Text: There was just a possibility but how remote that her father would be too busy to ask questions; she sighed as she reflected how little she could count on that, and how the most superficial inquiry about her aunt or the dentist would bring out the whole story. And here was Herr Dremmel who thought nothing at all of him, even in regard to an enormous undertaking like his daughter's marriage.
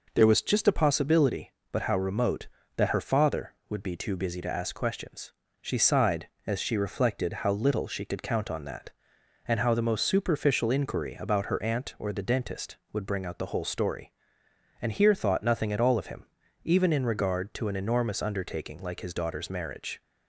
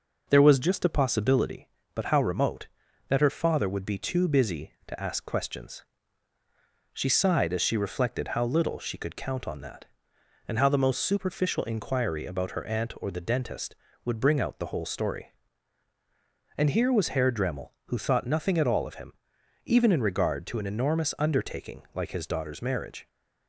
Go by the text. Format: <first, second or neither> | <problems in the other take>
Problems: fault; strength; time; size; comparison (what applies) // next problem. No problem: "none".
second | skips "was Herr Dremmel who"; at 15.1 s